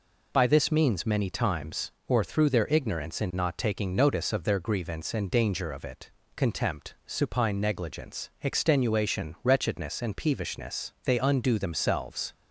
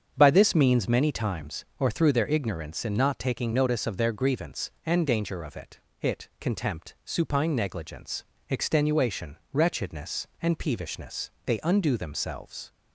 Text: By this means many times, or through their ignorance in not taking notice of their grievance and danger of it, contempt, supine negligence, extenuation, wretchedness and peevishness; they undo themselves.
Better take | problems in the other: first | starts louder than the rest; strong; until 1.1 s; 7.5 dB // says "it" twice; at 6.0 s

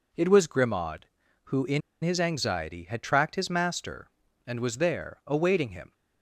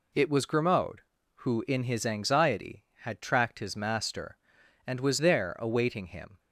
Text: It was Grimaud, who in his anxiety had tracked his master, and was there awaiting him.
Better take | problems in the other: second | pauses between "in" and "his"; slight; at 1.8 s; 0.22 s long

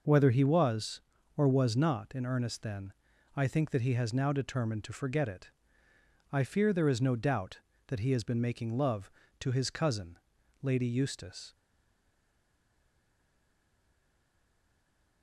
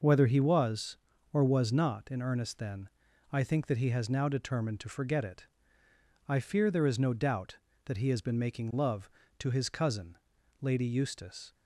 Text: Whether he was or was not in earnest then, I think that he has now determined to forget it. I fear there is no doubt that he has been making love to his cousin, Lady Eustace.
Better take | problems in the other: second | stays silent after the last word; strong; from 11.5 s on; 3.7 s long

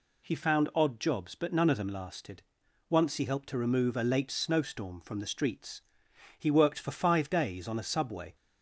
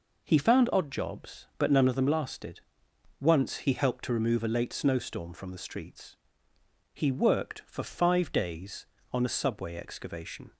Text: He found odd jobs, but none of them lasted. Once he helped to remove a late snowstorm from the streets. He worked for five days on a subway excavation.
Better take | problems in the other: second | stops before "excavation"; at 8.3 s

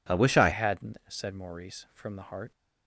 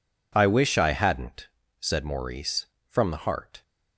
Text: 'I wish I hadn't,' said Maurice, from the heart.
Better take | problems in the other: second | changes voice at "hadn't"; from 0.5 s on; 2.0 s long

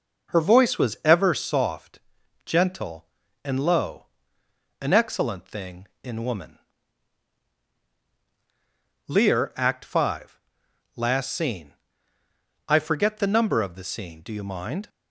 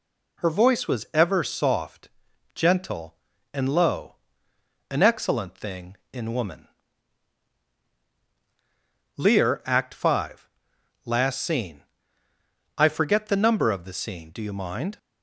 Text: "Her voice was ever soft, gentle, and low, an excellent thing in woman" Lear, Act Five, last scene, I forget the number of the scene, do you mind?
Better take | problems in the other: second | starts louder than the rest; noticeable; until 1.6 s; 5.5 dB // pauses between "woman" and "Lear"; strong; at 6.5 s; 2.4 s long; strong in the second

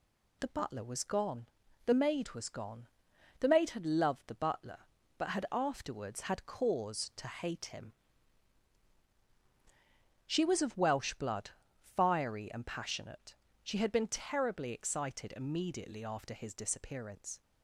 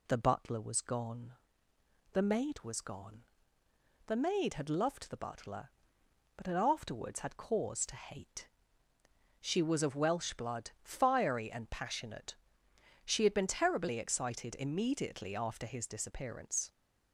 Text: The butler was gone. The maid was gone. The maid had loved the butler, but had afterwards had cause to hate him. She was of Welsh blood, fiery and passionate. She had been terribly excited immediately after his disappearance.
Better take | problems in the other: first | skips "him"; at 8.9 s

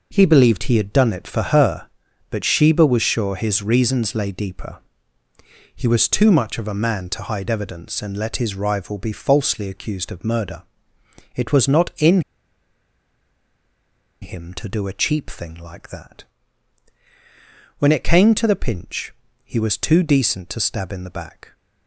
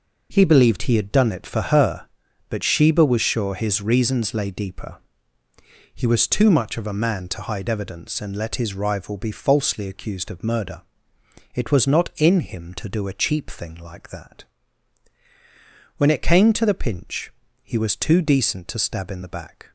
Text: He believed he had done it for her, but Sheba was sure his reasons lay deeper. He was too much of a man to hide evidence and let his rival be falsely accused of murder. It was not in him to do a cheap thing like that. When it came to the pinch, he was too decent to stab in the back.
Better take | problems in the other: second | pauses between "in" and "him"; strong; at 12.1 s; 2.0 s long

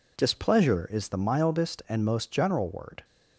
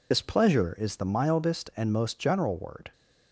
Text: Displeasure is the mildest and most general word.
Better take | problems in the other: first | loses the start of "Displeasure"; at 0.1 s; 50 ms

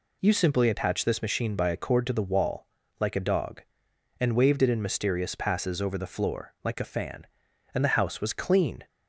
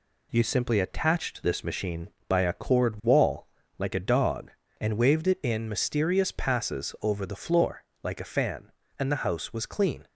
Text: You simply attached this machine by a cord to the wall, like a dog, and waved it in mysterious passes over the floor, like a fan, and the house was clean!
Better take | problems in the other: first | skips "to the"; at 3.0 s

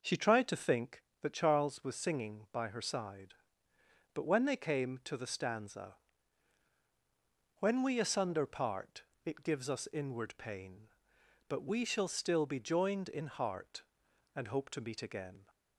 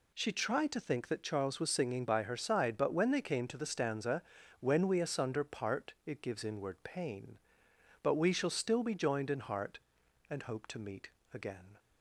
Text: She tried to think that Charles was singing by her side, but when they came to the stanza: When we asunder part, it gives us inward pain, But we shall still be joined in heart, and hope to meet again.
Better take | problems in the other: first | skips "us"; at 6.4 s // pauses between "meet" and "again"; slight; at 11.0 s; 0.24 s long

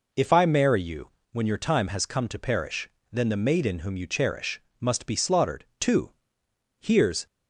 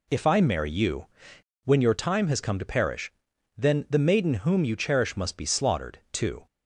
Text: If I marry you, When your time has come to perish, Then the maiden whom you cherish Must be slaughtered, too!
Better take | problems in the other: second | pauses between "cherish" and "Must"; slight; at 4.5 s; 0.18 s long // goes on to say "Here's"; slight; from 6.8 s on; 0.44 s long

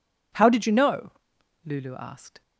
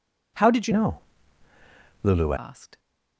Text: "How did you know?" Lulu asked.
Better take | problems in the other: first | changes voice from "know" to "Lulu"; from 0.7 to 2.3 s; 1.6 s long

